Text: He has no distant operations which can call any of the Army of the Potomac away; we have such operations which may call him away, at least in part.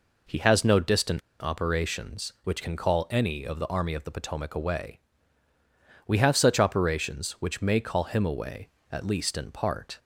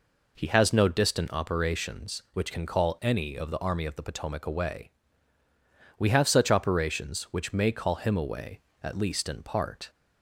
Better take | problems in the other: second | pauses between "distant" and "operations"; slight; at 1.2 s; 0.21 s long

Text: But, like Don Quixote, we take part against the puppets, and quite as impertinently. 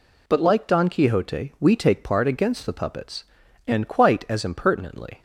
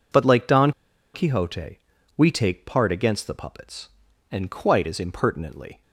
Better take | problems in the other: first | pauses between "Don" and "Quixote"; at 0.7 s; 0.43 s long

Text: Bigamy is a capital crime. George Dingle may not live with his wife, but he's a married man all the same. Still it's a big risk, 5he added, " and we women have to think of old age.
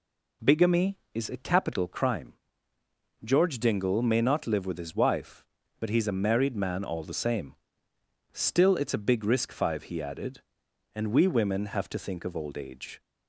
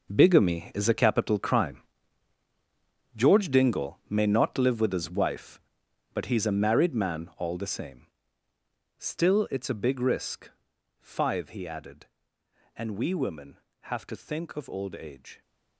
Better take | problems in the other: first | gets quieter; strong; throughout; 15 dB

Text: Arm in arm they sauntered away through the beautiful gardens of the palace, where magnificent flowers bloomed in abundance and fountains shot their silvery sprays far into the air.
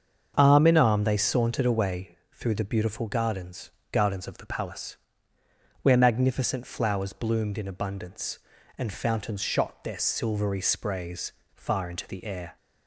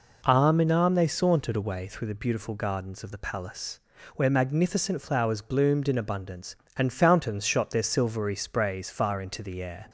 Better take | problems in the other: second | starts louder than the rest; until 1.3 s; 7 dB // pauses between "away" and "through"; slight; at 2.1 s; 0.16 s long // says "gardens" twice; at 3.9 s // pauses between "sprays" and "far"; slight; at 11.3 s; 0.23 s long

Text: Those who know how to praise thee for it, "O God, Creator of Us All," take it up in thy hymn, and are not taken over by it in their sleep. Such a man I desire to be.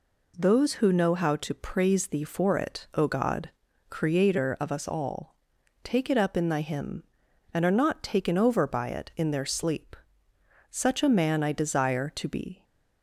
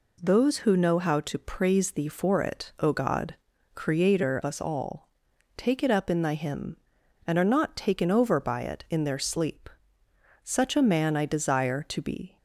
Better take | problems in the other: first | skips "of"; at 4.4 s

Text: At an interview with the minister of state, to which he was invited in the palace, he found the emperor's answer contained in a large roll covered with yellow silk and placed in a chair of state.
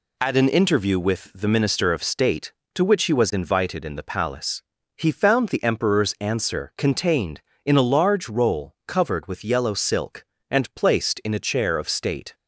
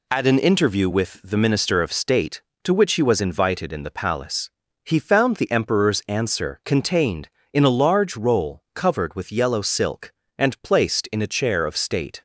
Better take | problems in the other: neither | none

